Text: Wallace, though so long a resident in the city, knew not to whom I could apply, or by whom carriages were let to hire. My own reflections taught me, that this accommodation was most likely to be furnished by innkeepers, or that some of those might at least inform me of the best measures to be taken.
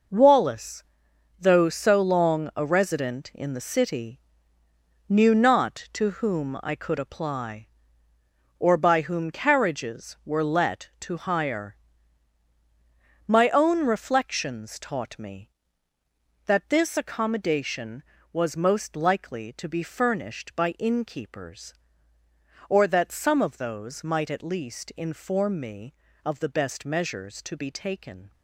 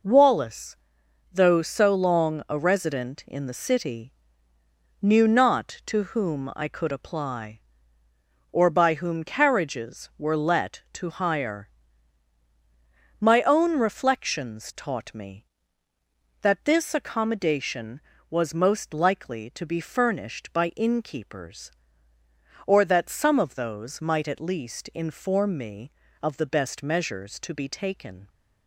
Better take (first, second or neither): second